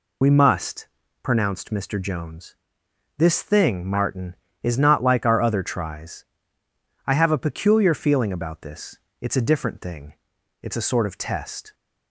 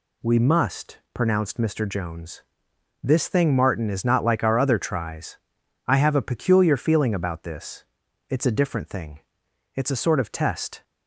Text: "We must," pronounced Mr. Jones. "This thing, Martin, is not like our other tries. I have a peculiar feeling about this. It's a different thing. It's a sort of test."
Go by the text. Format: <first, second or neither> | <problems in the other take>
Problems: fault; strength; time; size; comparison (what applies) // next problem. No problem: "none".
second | loses the start of "We"; at 0.2 s; 55 ms